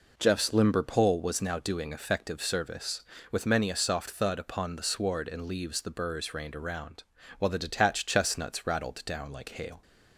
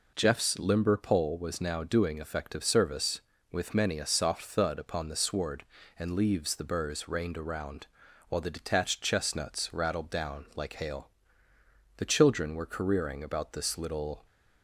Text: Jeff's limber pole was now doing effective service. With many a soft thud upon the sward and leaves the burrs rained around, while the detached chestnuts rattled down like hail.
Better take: first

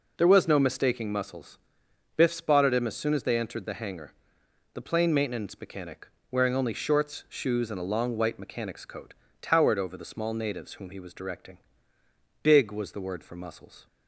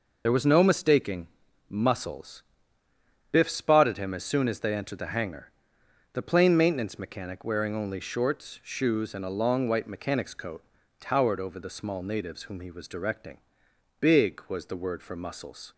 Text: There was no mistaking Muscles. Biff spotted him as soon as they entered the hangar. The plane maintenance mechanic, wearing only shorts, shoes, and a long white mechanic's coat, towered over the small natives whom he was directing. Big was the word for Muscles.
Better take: first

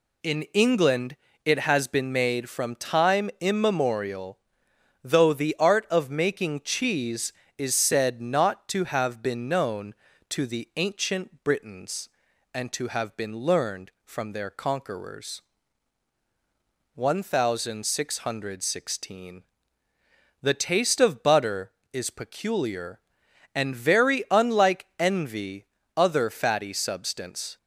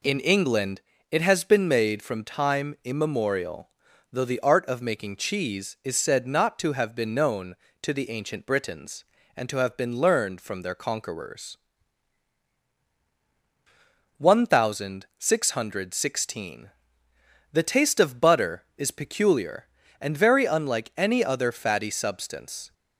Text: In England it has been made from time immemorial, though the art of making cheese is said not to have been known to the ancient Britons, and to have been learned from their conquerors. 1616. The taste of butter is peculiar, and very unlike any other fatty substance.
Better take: second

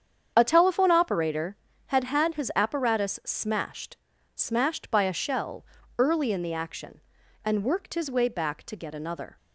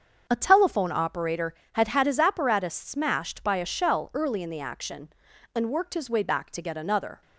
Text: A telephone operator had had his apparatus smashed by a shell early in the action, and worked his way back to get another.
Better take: second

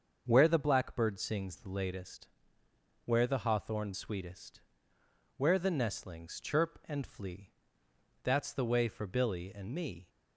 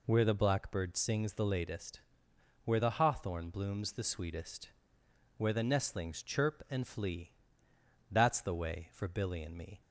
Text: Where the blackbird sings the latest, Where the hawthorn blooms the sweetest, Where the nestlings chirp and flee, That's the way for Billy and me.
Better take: second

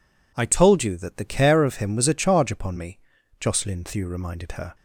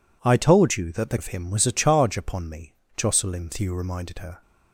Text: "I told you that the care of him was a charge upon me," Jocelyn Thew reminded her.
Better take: first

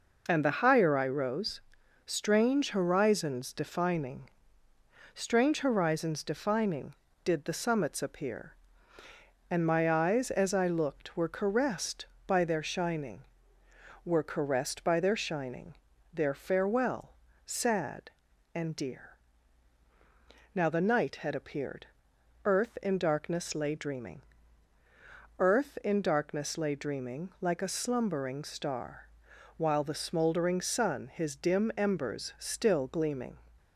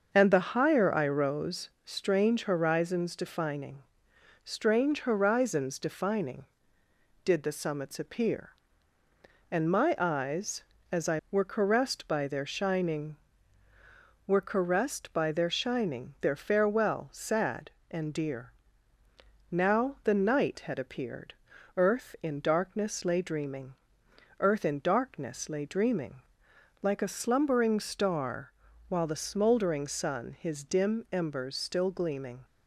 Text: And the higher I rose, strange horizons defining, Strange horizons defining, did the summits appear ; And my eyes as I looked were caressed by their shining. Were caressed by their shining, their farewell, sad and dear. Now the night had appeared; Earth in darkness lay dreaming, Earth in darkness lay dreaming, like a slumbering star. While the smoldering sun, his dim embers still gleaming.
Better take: first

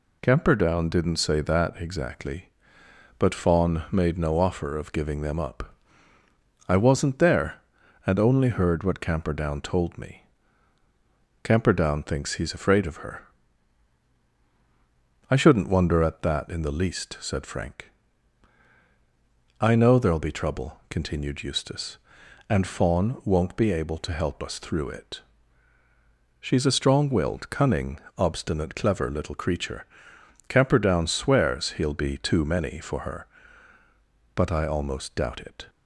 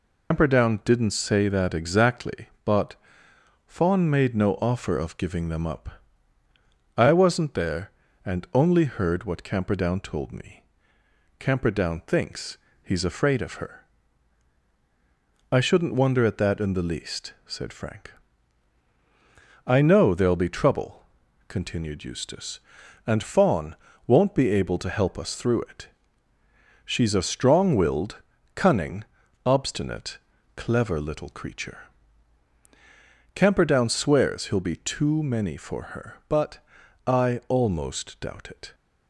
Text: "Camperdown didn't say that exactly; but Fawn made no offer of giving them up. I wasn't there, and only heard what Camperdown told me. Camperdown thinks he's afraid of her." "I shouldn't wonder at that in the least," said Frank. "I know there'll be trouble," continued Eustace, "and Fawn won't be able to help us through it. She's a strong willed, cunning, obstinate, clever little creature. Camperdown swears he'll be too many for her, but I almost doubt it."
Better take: first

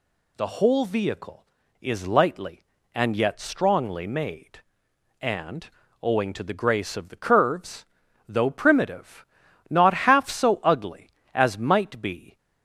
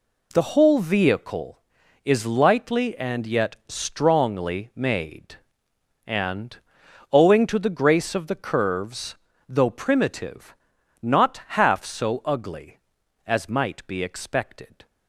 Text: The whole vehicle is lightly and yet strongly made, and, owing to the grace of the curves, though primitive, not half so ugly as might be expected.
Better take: second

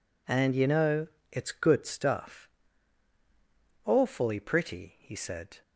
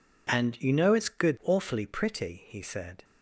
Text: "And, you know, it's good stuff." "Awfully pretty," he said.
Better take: first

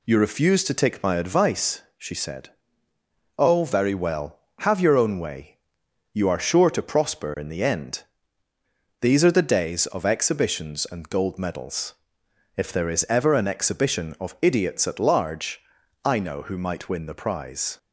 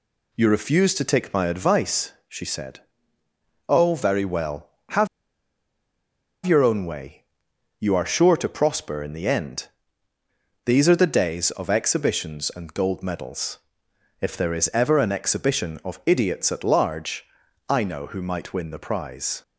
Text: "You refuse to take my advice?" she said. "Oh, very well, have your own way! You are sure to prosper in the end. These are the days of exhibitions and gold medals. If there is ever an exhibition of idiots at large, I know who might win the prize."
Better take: first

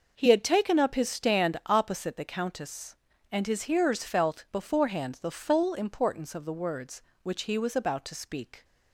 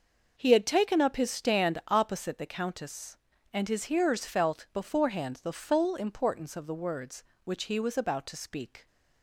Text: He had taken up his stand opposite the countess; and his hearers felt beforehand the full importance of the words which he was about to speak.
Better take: neither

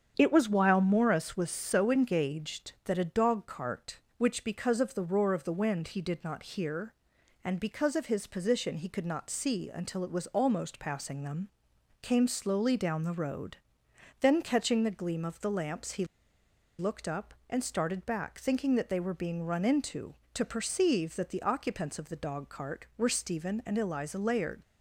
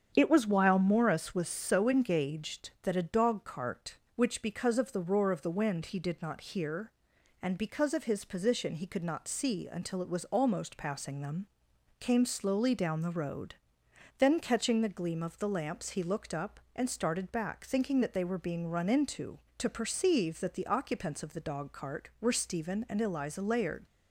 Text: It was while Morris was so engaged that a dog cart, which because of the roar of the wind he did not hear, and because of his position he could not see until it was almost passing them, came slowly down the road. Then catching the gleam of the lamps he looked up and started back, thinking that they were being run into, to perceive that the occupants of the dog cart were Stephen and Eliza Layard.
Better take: second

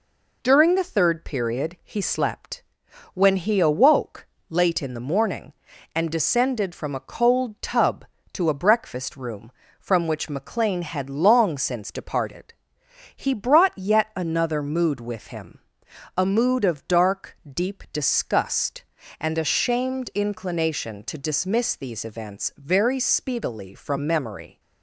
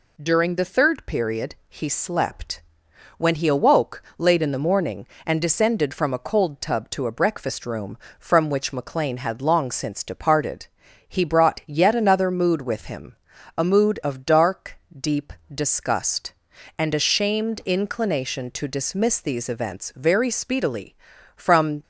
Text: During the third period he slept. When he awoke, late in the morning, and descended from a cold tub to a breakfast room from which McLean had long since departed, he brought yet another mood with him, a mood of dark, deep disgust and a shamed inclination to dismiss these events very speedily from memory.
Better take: first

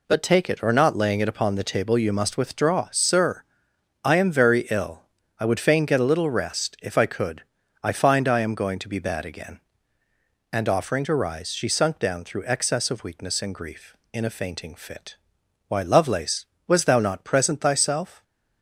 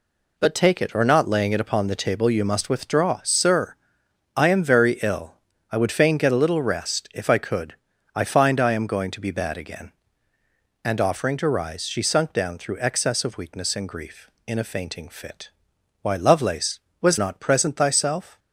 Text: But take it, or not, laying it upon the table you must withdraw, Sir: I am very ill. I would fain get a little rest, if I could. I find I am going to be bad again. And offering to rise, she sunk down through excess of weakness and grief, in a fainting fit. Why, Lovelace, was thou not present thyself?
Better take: first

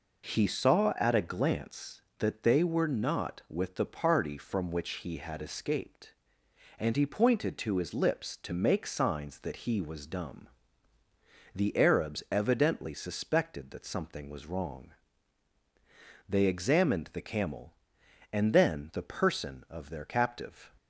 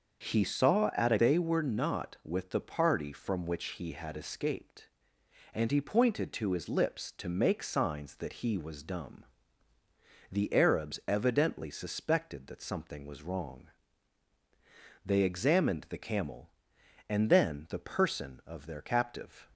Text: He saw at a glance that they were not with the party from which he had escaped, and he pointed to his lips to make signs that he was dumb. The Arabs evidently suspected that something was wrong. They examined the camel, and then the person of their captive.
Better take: first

